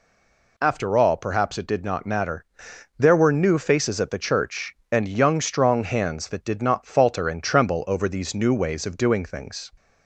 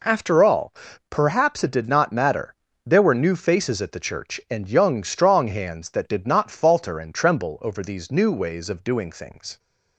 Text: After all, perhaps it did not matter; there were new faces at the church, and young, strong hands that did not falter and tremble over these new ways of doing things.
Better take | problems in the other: second | stays silent before the first word; slight; until 0.5 s; 0.5 s long

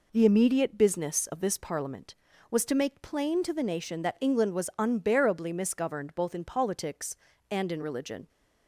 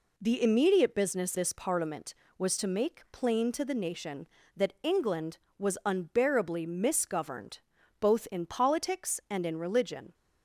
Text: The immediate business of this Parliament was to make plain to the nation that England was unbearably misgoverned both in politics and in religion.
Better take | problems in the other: first | skips "of"; at 1.3 s // pauses between "misgoverned" and "both"; at 7.5 s; 0.40 s long

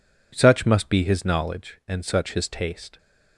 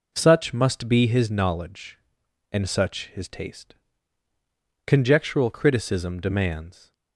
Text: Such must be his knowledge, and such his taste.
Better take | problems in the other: first | goes on to say "Conjectural criticism demands"; strong; from 4.8 s on; 2.0 s long

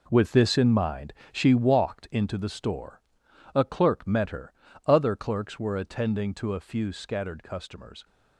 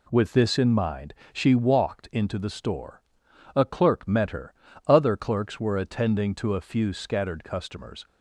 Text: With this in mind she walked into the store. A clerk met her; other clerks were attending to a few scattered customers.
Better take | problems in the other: second | gets quieter; strong; throughout; 10.5 dB // pauses between "mind" and "she"; slight; at 1.1 s; 0.20 s long; slight in the second

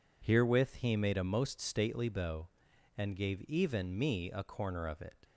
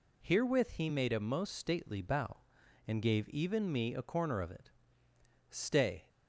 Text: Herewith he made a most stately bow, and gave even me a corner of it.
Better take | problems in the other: first | goes on to say "Stay"; from 5.4 s on; 0.60 s long

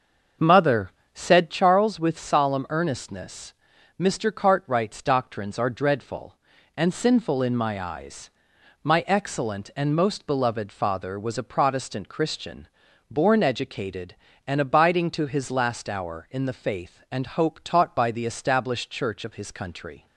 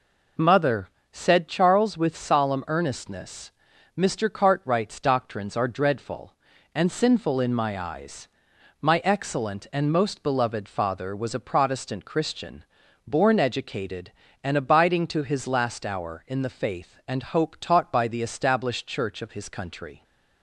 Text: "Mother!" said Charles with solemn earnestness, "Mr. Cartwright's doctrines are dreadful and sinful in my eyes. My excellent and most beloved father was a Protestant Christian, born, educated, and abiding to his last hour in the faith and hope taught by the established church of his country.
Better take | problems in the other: second | starts louder than the rest; until 1.7 s; 6.5 dB

